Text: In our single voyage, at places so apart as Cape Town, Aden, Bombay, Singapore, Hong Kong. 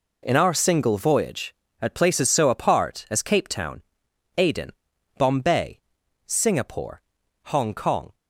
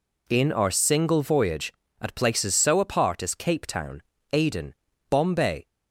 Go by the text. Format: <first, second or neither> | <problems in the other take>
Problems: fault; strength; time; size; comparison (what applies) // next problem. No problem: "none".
first | stops before "Singapore Hong Kong"; at 5.6 s